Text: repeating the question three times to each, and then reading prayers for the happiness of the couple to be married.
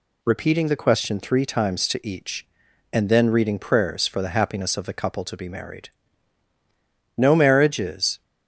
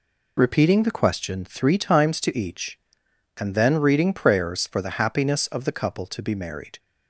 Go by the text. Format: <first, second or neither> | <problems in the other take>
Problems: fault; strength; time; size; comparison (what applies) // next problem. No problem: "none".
second | goes on to say "No marriage is"; noticeable; from 7.1 s on; 1.0 s long